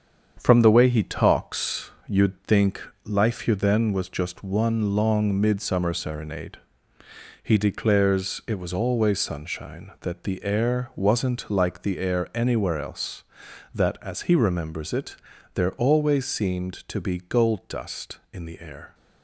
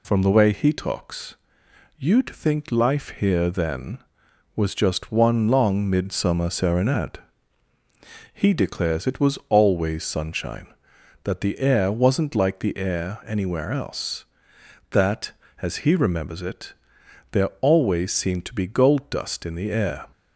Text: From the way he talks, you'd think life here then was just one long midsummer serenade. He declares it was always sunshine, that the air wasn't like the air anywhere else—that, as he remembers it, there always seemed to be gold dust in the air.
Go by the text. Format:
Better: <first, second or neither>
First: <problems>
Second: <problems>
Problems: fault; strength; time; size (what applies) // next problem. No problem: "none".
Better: second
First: gets quieter; noticeable; throughout; 6 dB // pauses between "think" and "life"; slight; at 2.7 s; 0.24 s long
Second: none